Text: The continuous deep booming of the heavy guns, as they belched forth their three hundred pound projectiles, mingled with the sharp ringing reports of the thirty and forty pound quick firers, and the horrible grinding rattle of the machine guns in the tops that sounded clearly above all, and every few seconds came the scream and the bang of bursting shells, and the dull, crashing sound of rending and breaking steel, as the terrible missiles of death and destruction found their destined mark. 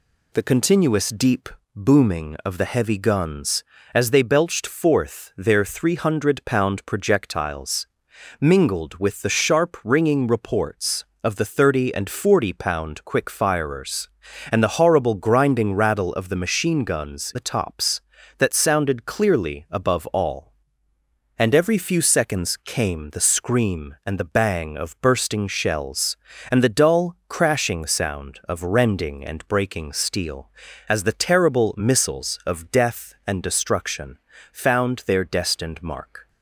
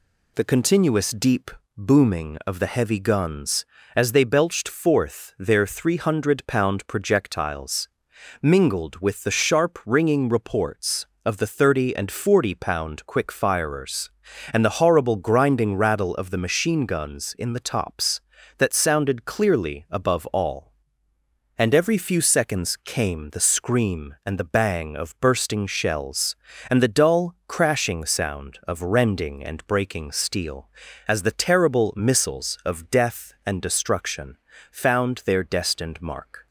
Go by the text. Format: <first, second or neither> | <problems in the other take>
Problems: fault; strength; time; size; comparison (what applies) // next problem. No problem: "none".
second | pauses between "deep" and "booming"; slight; at 1.5 s; 0.26 s long; slight in the second // skips "in"; at 17.3 s // pauses between "destruction" and "found"; slight; at 34.1 s; 0.36 s long; slight in the second